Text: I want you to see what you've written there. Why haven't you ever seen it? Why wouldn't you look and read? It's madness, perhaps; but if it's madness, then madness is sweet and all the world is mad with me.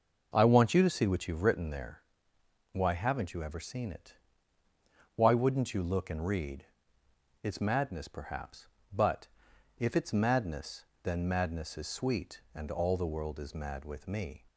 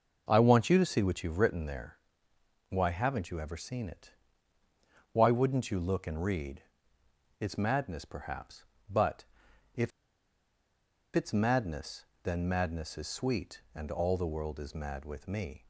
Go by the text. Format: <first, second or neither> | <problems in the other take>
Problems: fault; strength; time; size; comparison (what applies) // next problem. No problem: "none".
first | pauses between "but" and "if"; noticeable; at 9.2 s; 0.50 s long; noticeable in the first // pauses between "if" and "it's"; strong; at 9.9 s; 1.2 s long